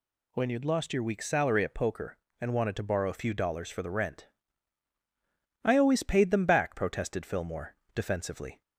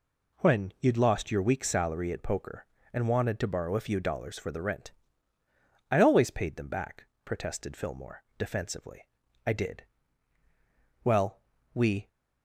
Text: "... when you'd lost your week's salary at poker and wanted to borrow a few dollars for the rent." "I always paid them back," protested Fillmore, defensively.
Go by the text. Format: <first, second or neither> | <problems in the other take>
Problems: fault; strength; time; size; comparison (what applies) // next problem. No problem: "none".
first | goes on to say "I did Well we"; strong; from 9.4 s on; 2.6 s long